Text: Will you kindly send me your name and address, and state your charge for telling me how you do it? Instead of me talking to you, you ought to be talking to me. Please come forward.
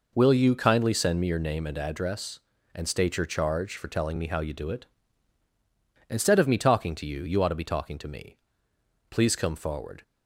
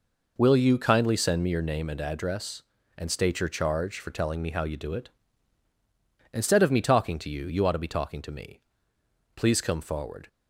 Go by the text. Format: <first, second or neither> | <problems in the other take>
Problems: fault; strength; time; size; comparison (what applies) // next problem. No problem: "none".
neither | none